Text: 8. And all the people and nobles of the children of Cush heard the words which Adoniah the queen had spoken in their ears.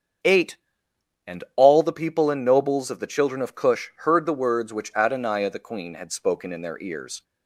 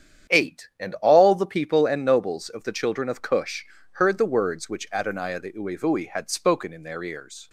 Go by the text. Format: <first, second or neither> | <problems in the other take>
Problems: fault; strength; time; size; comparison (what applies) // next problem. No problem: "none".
first | starts louder than the rest; strong; until 1.4 s; 9 dB; strong in the first // pauses between "Cush" and "heard"; slight; at 3.6 s; 0.26 s long // says "uevui" for "queen"; at 5.5 s